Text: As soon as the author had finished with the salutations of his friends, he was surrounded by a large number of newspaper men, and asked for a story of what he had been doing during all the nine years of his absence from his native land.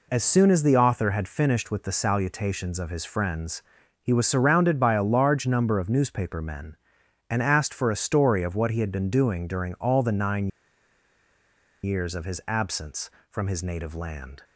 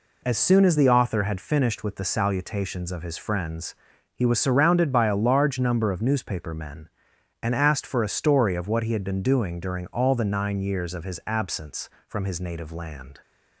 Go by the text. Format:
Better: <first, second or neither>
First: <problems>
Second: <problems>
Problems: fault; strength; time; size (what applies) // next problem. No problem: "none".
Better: second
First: pauses between "nine" and "years"; strong; at 10.4 s; 1.3 s long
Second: none